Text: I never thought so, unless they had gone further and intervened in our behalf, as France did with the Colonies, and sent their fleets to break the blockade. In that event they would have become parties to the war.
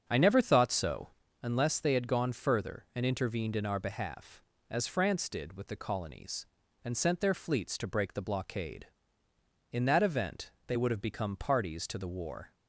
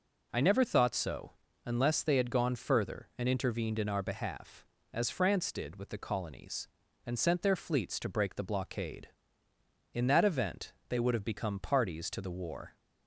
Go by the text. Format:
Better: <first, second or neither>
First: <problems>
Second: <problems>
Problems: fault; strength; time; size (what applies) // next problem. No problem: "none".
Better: second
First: starts louder than the rest; until 1.4 s; 7 dB // pauses between "event" and "they"; slight; at 10.5 s; 0.16 s long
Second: pauses between "event" and "they"; slight; at 10.7 s; 0.16 s long